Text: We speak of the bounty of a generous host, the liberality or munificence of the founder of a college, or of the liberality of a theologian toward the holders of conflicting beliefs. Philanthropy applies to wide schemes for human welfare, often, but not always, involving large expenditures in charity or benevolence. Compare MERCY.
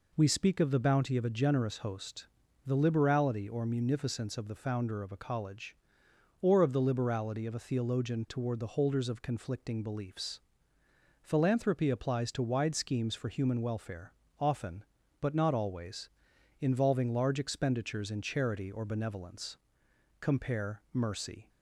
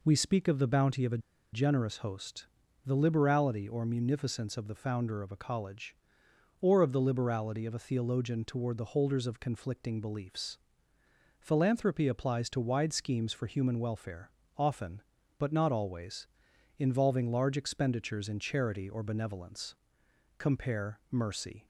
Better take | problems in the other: first | pauses between "a" and "generous"; slight; at 1.1 s; 0.34 s long

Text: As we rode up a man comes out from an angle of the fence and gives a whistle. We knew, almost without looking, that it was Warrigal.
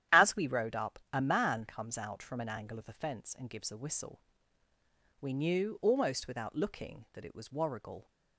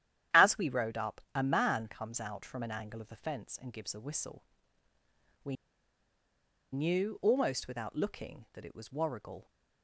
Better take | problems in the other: first | starts louder than the rest; strong; until 1.4 s; 11 dB; strong in the first // pauses between "up" and "a"; slight; at 1.1 s; 0.16 s long; slight in the first // pauses between "We" and "knew"; at 5.5 s; 1.1 s long

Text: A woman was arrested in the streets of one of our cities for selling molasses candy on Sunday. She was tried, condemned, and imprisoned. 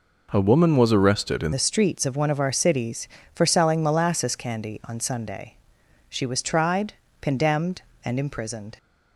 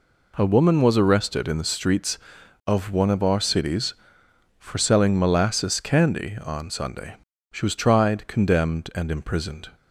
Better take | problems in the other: second | changes voice at "the"; from 1.5 s on; 7.2 s long

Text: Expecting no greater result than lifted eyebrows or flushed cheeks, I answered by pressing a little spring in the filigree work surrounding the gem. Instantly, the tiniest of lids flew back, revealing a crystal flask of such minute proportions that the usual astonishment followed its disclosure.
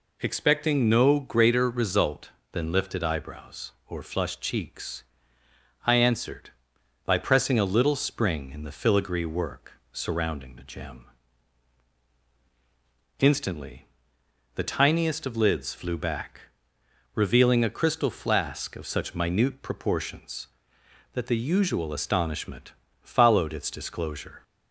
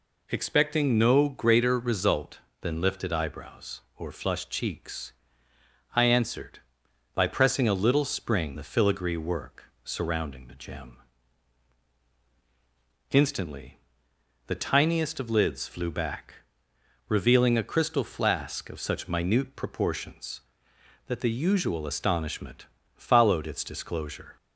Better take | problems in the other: first | skips "in"; at 8.5 s // pauses between "work" and "surrounding"; slight; at 9.6 s; 0.20 s long; slight in the first // pauses between "astonishment" and "followed"; slight; at 22.6 s; 0.32 s long; slight in the first

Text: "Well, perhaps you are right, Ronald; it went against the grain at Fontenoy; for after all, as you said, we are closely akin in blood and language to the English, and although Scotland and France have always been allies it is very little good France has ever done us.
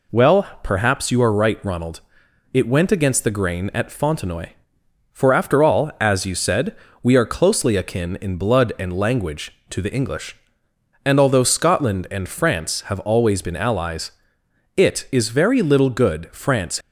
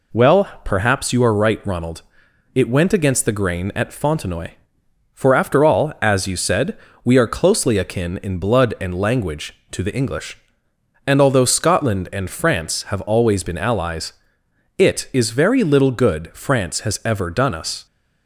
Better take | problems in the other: second | pauses between "allies" and "it"; noticeable; at 14.1 s; 0.66 s long; noticeable in the second // stops before "has ever done us"; at 16.8 s

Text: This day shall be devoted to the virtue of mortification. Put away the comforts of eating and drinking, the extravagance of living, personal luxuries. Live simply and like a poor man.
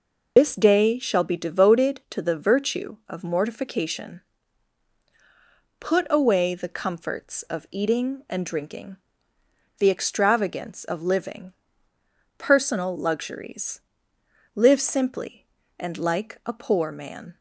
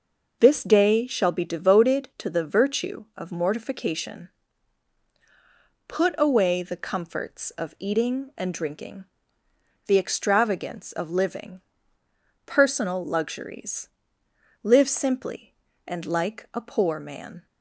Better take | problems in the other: second | loses the start of "This"; at 0.3 s; 45 ms

